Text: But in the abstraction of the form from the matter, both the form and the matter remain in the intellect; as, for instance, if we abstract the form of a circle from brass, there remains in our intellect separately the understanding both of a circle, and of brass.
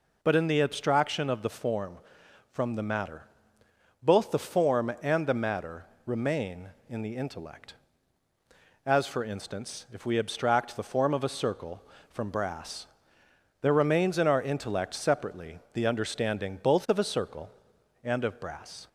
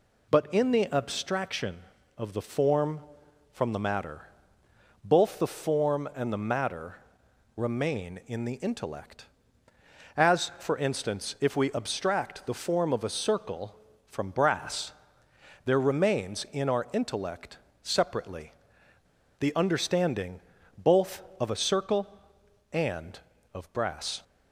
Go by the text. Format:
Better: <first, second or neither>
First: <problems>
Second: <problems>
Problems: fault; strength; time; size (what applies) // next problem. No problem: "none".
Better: first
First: pauses between "matter" and "remain"; slight; at 5.8 s; 0.20 s long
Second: pauses between "matter" and "remain"; noticeable; at 6.9 s; 0.58 s long // pauses between "intellect" and "separately"; slight; at 17.5 s; 0.24 s long // pauses between "separately" and "the"; noticeable; at 18.5 s; 0.86 s long // pauses between "understanding" and "both"; slight; at 20.4 s; 0.36 s long